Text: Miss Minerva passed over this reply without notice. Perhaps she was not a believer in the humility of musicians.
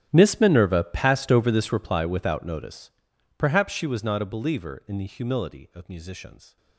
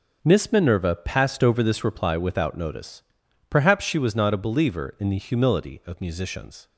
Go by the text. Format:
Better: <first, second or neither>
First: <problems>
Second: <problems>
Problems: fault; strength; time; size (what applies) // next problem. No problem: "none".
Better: second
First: gets quieter; strong; throughout; 20.5 dB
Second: none